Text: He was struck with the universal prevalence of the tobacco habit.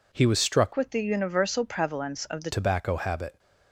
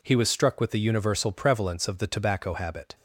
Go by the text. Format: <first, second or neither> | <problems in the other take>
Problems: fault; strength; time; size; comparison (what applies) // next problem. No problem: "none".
second | changes voice from "with" to "the"; from 0.7 to 2.5 s; 1.8 s long